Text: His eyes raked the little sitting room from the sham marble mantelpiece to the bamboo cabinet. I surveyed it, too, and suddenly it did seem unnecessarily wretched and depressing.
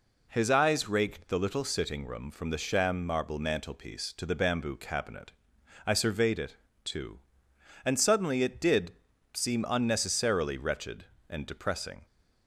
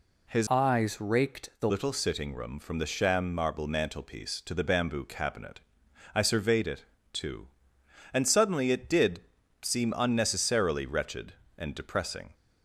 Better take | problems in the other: first | changes voice from "eyes" to "the"; from 0.5 to 1.7 s; 1.2 s long // pauses between "did" and "seem"; at 9.2 s; 0.40 s long; also in the first

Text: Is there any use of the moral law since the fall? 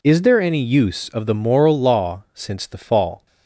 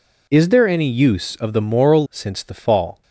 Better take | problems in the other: first | skips "law"; at 2.0 s

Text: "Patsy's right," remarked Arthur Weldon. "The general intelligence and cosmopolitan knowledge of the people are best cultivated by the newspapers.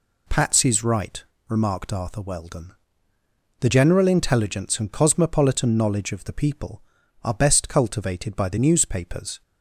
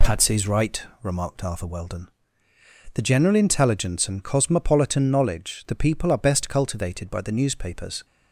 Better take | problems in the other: first | skips "of"; at 5.6 s

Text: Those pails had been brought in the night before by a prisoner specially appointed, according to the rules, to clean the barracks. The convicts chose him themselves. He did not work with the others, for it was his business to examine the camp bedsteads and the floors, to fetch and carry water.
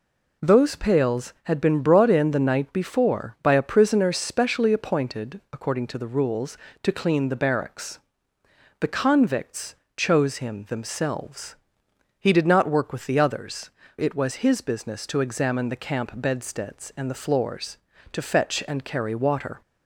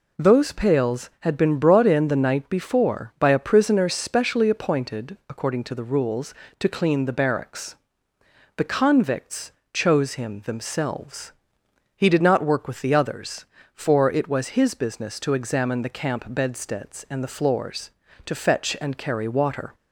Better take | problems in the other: second | pauses between "convicts" and "chose"; slight; at 9.7 s; 0.20 s long; slight in the second // skips "for"; at 13.8 s

